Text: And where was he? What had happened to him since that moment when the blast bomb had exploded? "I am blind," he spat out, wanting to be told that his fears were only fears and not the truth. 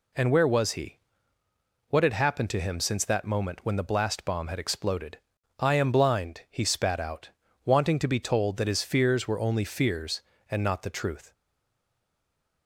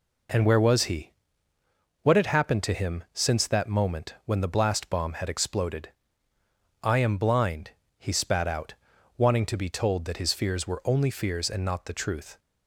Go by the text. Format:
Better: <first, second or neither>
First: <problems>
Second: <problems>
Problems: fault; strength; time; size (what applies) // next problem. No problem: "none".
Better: second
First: stays silent after the last word; noticeable; from 11.3 s on; 1.3 s long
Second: none